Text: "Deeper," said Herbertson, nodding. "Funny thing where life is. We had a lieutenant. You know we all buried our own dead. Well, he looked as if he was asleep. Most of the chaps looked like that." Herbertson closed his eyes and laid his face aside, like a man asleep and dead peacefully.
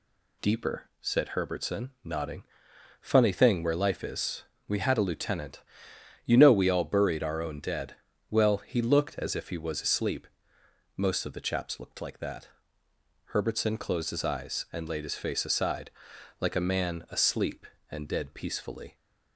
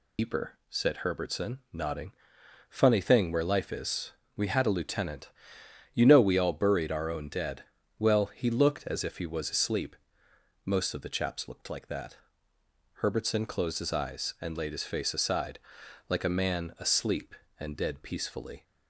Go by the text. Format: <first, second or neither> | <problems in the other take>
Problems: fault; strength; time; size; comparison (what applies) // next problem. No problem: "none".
first | loses the start of "Deeper"; at 0.1 s; 100 ms